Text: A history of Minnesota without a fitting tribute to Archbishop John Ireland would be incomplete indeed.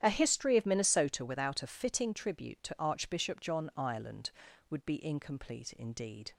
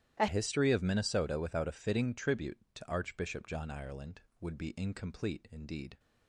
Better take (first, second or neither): first